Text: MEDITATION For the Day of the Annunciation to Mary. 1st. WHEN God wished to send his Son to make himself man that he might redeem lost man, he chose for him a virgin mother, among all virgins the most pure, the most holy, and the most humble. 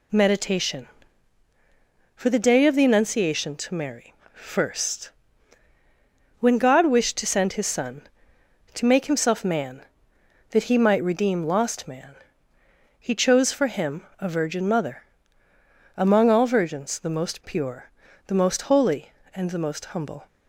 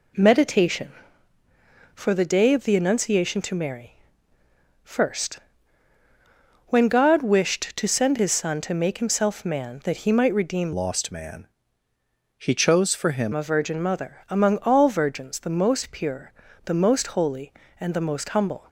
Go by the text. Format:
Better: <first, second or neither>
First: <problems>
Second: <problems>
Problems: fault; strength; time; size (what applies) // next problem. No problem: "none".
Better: first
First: none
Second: changes voice from "lost" to "him"; from 10.7 to 13.3 s; 2.6 s long